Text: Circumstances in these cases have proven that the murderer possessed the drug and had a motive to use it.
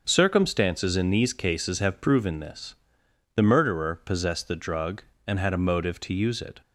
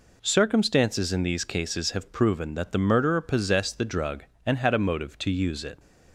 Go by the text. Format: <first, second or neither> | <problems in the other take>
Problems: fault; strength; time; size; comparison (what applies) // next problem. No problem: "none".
second | starts louder than the rest; until 1.0 s; 6 dB // says "this" for "that"; at 2.3 s